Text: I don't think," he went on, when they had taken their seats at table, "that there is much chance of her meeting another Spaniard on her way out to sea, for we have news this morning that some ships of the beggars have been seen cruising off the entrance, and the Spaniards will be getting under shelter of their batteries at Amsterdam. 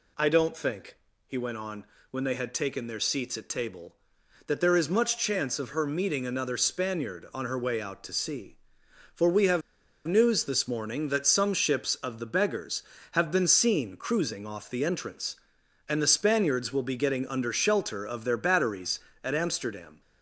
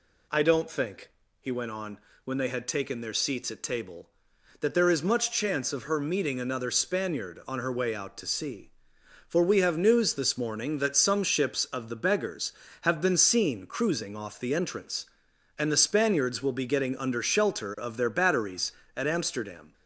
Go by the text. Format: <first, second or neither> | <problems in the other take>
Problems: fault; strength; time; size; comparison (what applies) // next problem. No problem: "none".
second | pauses between "have" and "news"; noticeable; at 9.6 s; 0.46 s long